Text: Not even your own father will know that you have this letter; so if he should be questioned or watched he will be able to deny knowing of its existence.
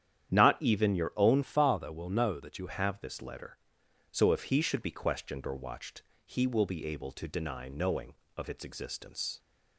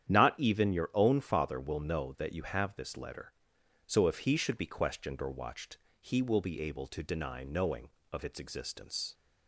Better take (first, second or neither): second